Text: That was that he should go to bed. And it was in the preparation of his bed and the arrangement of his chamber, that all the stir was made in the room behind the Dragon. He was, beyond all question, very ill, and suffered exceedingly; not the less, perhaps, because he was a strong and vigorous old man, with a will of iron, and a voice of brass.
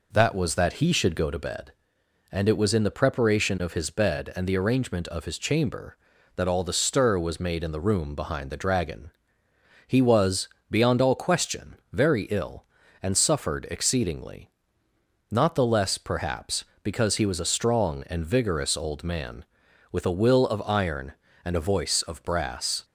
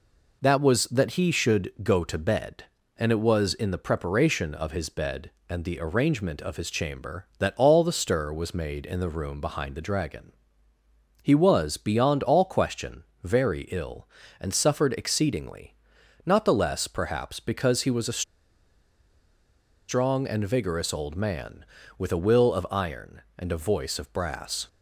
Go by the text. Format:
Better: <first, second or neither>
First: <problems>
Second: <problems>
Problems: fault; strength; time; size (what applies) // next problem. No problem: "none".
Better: first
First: none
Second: pauses between "a" and "strong"; strong; at 18.2 s; 1.6 s long